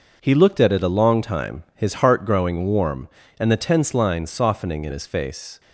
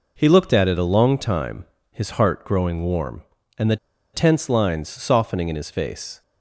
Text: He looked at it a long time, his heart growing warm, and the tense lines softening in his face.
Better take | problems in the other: first | pauses between "the" and "tense"; at 3.7 s; 0.36 s long

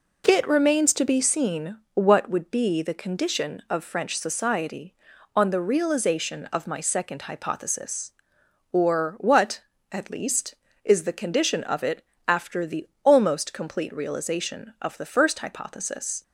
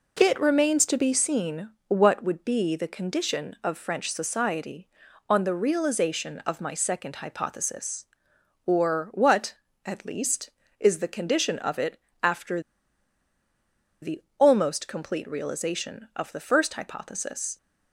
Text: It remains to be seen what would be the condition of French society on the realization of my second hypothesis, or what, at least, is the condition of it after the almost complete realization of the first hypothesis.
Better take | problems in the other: first | pauses between "seen" and "what"; slight; at 1.6 s; 0.16 s long // pauses between "it" and "after"; slight; at 11.9 s; 0.24 s long; slight in the first // pauses between "after" and "the"; strong; at 12.5 s; 1.4 s long // pauses between "the" and "almost"; slight; at 14.2 s; 0.16 s long; slight in the first

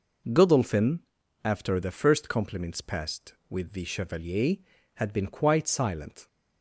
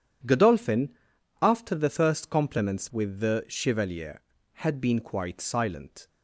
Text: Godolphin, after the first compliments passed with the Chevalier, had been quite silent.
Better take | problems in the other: first | skips "passed"; at 2.8 s

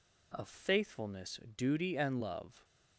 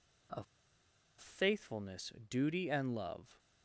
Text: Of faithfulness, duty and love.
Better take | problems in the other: first | pauses between "Of" and "faithfulness"; noticeable; at 0.4 s; 0.75 s long

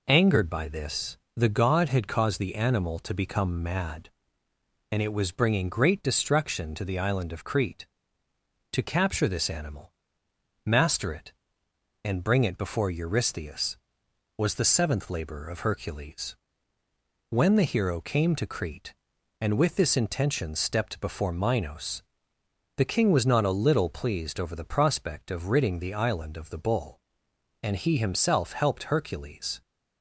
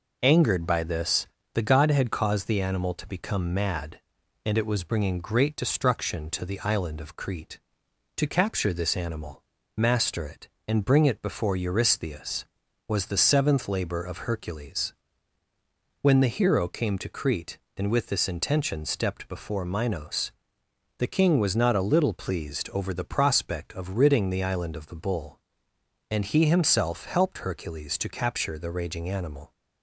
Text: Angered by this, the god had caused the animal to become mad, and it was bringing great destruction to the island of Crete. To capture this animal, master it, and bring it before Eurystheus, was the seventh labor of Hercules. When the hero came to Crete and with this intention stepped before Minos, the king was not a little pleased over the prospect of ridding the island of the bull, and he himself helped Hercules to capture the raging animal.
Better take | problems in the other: second | stops before "to capture the raging animal"; at 29.6 s

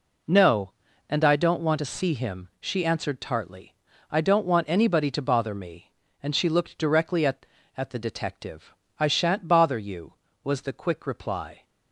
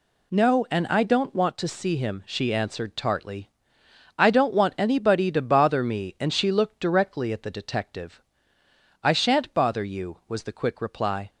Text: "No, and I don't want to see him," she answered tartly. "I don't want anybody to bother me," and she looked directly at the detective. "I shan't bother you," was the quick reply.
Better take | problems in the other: second | says "at" twice; at 7.7 s

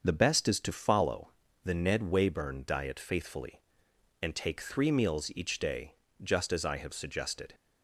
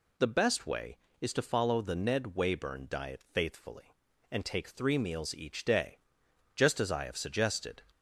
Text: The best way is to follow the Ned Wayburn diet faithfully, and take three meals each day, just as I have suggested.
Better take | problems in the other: second | starts louder than the rest; until 1.0 s; 6.5 dB // skips "way"; at 0.4 s // pauses between "follow" and "the"; slight; at 1.3 s; 0.32 s long

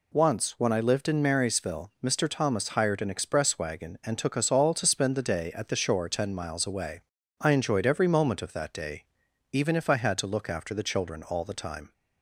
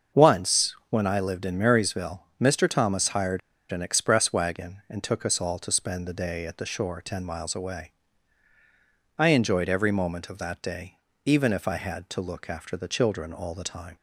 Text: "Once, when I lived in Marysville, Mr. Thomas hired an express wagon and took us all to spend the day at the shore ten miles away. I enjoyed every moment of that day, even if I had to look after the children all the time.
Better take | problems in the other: first | starts louder than the rest; until 1.2 s; 6.5 dB // pauses between "hired" and "an"; slight; at 3.4 s; 0.31 s long

